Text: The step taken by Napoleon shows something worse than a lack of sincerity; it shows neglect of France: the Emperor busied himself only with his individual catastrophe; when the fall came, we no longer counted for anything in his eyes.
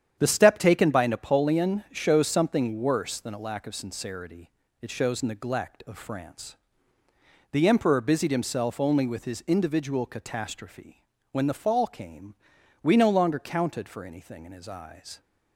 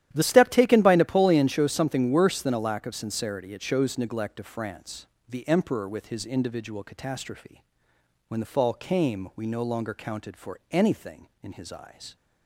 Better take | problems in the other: first | starts louder than the rest; strong; until 1.1 s; 12 dB; strong in the first // skips "busied himself only"; at 5.8 s

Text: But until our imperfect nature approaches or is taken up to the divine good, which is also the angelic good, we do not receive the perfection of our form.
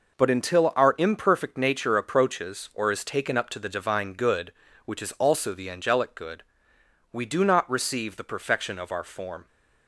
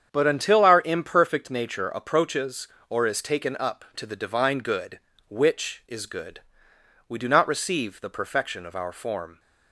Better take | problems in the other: first | starts louder than the rest; strong; until 1.1 s; 8 dB // skips "also the angelic"; at 6.0 s

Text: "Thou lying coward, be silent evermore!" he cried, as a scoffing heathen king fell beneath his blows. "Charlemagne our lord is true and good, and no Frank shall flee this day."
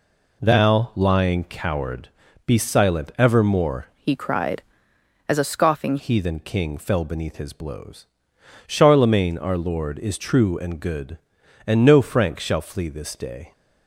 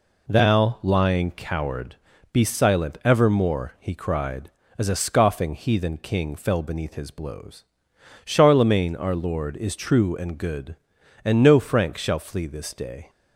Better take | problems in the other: second | changes voice from "he" to "scoffing"; from 3.9 to 5.9 s; 2.0 s long

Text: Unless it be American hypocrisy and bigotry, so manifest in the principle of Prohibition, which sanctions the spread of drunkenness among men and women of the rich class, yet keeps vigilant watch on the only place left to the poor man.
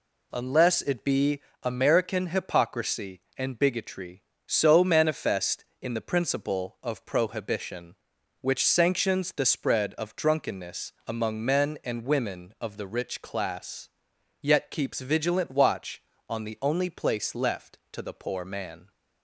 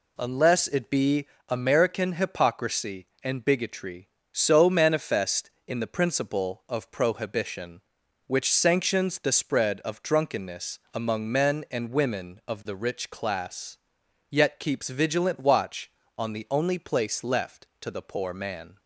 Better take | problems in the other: neither | pauses between "be" and "American"; slight; the same in both

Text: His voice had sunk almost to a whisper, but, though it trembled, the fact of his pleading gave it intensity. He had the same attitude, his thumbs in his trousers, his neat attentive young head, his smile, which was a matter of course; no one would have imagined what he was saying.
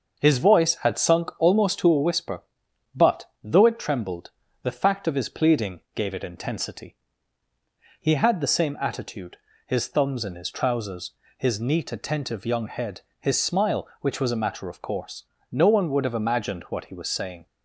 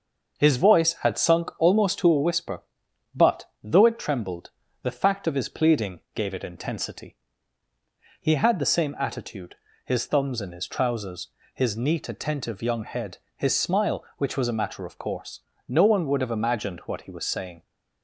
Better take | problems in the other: neither | starts louder than the rest; the same in both

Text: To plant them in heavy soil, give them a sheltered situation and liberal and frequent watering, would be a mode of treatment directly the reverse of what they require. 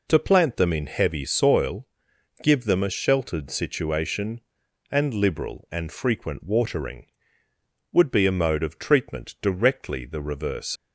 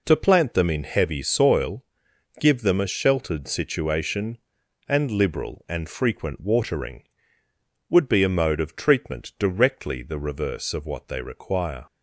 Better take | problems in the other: second | stops before "of what they require"; at 10.7 s

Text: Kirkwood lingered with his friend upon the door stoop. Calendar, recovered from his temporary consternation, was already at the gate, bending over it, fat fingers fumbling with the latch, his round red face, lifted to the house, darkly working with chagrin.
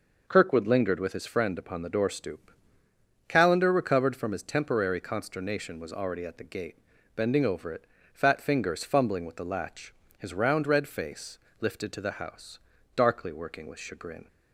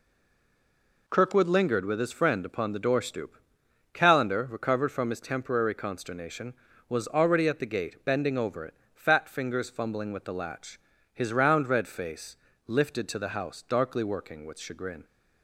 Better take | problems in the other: first | stays silent before the first word; until 1.0 s; 1.0 s long

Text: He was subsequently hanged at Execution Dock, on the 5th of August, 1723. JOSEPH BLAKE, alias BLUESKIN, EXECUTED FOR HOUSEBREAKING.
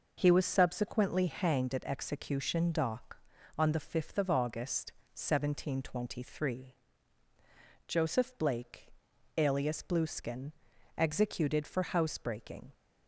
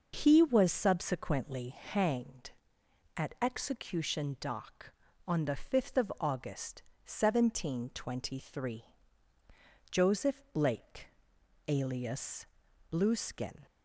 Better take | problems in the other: first | pauses between "alias" and "BLUESKIN"; noticeable; at 12.4 s; 0.46 s long // stops before "EXECUTED FOR HOUSEBREAKING"; at 13.6 s

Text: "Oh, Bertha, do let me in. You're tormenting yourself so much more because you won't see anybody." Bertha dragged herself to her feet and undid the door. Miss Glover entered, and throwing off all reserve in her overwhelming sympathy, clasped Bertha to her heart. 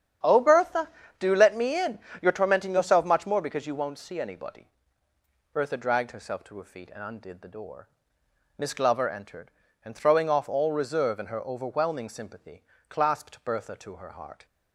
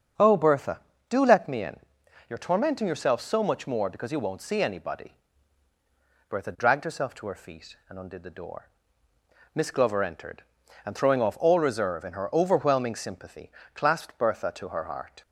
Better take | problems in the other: second | starts louder than the rest; strong; until 1.5 s; 9 dB; strong in the second // skips "so"; at 3.0 s

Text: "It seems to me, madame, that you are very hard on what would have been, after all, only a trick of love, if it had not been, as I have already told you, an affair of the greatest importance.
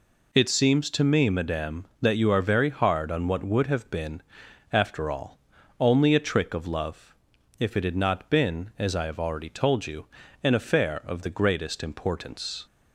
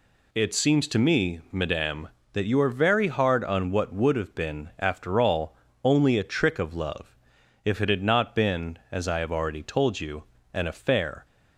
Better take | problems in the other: first | stops before "of the greatest importance"; at 11.2 s

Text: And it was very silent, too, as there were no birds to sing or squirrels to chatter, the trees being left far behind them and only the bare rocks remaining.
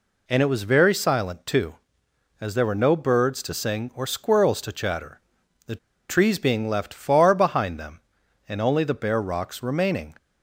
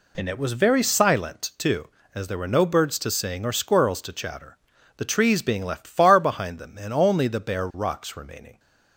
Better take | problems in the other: second | pauses between "the" and "trees"; slight; at 5.7 s; 0.32 s long

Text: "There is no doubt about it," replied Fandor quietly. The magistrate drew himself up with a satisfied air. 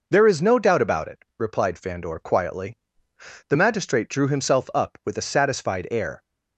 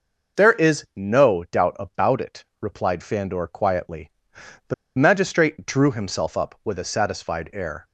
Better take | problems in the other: first | pauses between "The" and "magistrate"; slight; at 4.7 s; 0.23 s long

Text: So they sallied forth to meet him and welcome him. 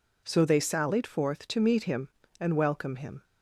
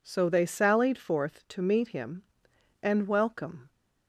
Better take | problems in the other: first | stops before "him"; at 3.6 s

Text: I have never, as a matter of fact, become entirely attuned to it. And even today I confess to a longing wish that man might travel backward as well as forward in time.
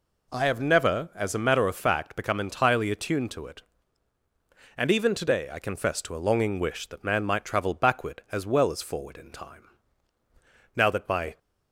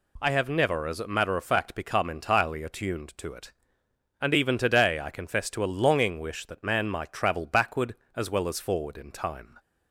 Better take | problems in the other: second | goes on to say "Now that my"; noticeable; from 10.7 s on; 0.62 s long

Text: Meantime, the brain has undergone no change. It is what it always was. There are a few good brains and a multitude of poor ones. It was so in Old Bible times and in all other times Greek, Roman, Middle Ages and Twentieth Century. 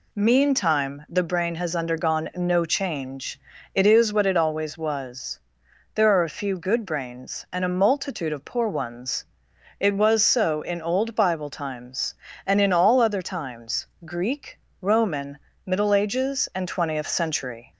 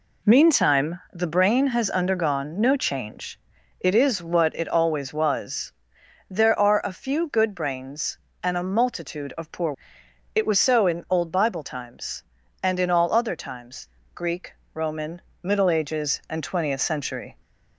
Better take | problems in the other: first | skips "ones"; at 10.0 s // pauses between "times" and "Greek"; slight; at 13.8 s; 0.26 s long; slight in the first

